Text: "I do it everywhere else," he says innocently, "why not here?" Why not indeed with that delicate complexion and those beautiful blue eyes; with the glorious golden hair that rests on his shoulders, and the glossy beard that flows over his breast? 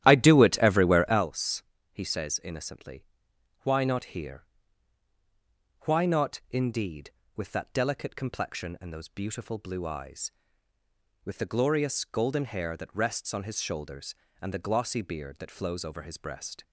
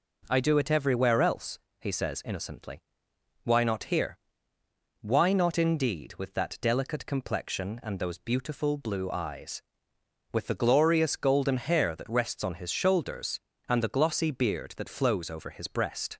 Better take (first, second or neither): second